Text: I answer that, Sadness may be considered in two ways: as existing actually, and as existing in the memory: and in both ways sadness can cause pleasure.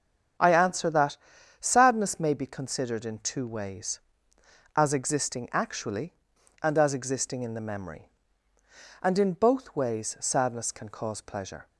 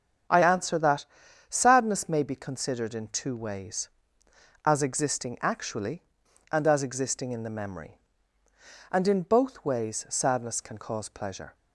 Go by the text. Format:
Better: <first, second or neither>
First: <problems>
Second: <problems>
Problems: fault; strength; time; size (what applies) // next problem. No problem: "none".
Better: neither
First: starts louder than the rest; strong; until 1.8 s; 7.5 dB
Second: starts louder than the rest; strong; until 1.7 s; 7.5 dB